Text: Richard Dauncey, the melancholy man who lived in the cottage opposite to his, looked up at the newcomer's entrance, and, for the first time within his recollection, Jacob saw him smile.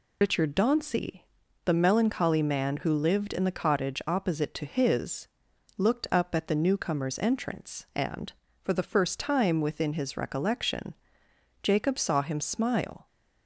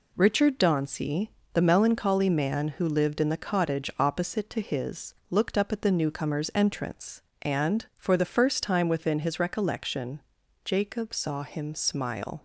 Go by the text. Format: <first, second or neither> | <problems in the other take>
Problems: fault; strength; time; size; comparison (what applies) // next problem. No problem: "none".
second | loses the start of "Richard"; at 0.2 s; 115 ms